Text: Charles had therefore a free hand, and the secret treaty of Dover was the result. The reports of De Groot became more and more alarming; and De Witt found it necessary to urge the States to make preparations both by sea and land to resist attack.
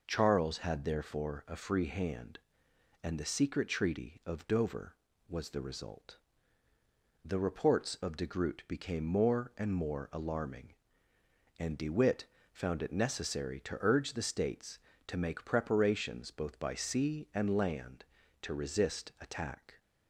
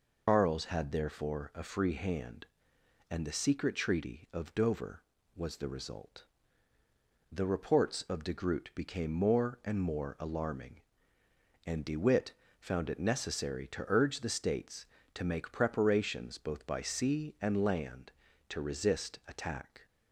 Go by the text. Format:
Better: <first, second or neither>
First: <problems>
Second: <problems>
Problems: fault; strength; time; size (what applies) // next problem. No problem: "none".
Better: first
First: pauses between "Witt" and "found"; slight; at 12.2 s; 0.26 s long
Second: loses the start of "Charles"; at 0.2 s; 150 ms // pauses between "Witt" and "found"; slight; at 12.3 s; 0.26 s long